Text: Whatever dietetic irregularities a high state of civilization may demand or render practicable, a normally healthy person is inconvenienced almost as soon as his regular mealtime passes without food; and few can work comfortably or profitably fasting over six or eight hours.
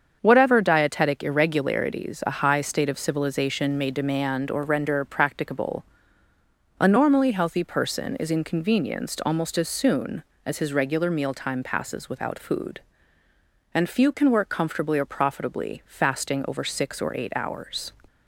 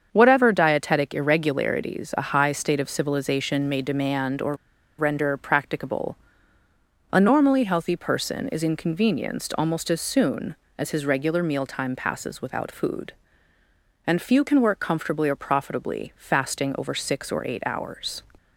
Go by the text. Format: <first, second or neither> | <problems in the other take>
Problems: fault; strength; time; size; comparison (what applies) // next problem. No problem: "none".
first | starts louder than the rest; strong; until 1.1 s; 7 dB; strong in the first // pauses between "or" and "render"; at 4.5 s; 0.44 s long